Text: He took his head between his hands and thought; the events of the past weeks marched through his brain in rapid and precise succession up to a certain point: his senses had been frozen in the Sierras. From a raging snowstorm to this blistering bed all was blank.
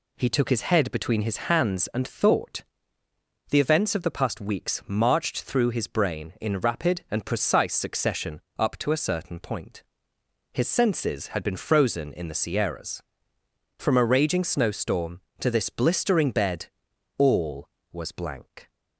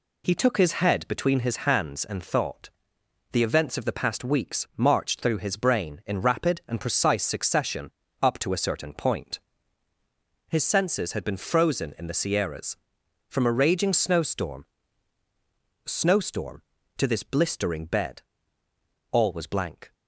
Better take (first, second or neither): first